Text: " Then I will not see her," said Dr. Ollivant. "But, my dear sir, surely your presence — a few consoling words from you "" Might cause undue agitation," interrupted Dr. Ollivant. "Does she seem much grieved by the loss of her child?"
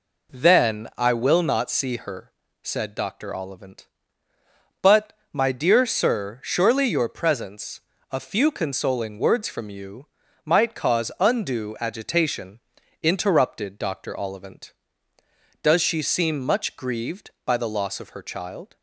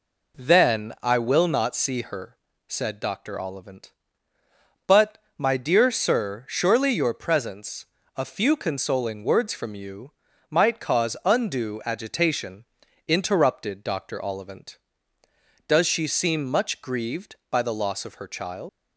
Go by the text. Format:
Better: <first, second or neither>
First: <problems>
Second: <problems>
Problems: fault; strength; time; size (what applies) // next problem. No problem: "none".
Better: first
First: none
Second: leaves "child" unfinished; at 18.6 s; 125 ms